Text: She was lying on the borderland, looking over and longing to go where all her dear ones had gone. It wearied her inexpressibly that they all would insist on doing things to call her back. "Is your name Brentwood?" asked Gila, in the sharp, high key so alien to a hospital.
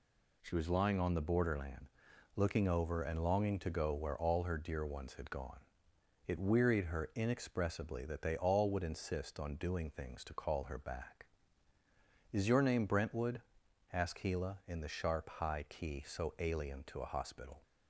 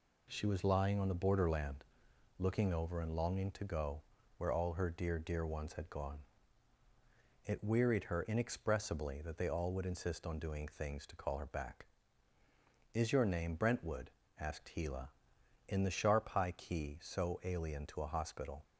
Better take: first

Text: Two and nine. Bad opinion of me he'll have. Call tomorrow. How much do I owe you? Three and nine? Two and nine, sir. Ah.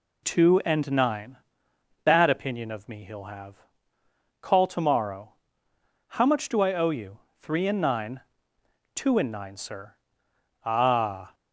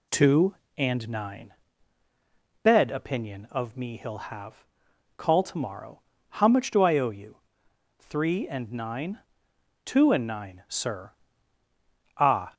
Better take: first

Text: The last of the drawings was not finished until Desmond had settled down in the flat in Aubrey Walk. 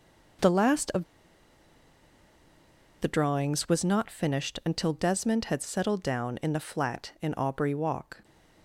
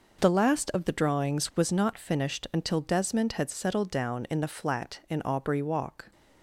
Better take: second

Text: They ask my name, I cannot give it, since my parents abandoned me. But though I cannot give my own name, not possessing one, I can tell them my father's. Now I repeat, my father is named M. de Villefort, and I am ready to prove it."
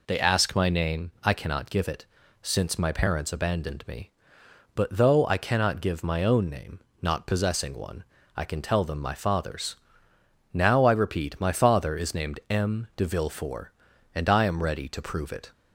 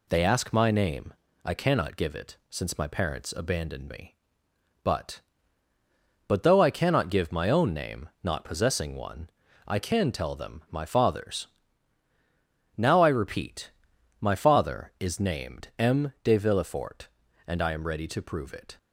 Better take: first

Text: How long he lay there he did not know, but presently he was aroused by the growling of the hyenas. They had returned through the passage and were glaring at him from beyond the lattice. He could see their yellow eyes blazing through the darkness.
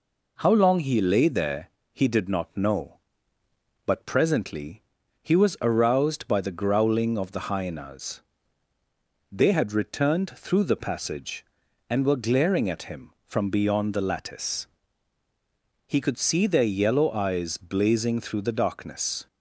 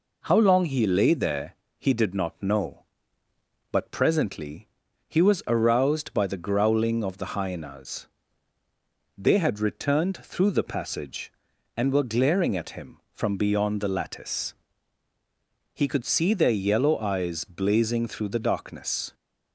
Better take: neither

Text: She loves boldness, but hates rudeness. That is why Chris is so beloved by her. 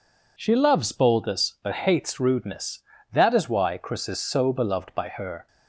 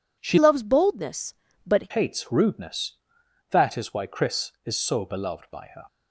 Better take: first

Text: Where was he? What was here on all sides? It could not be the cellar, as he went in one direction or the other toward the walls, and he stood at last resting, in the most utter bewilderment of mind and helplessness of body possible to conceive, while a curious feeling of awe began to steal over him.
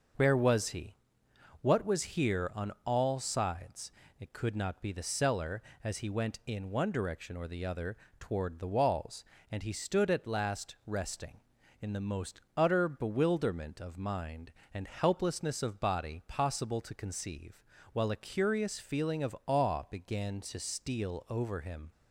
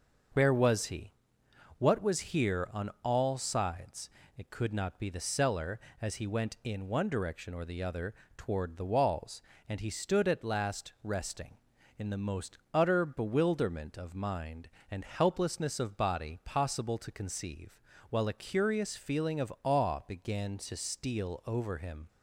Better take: neither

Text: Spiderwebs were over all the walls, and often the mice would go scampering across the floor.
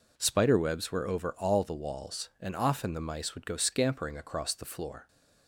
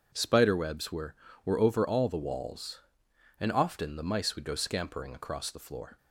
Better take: first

